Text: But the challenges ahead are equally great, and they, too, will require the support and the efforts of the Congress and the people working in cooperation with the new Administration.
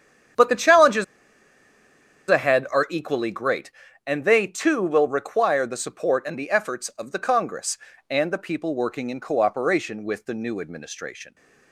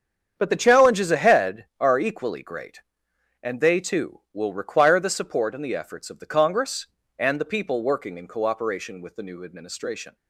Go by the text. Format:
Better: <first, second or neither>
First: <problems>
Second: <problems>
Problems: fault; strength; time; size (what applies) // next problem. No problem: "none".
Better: second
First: starts louder than the rest; strong; until 2.6 s; 9 dB // pauses between "challenges" and "ahead"; at 1.0 s; 1.2 s long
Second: starts louder than the rest; strong; until 1.3 s; 8 dB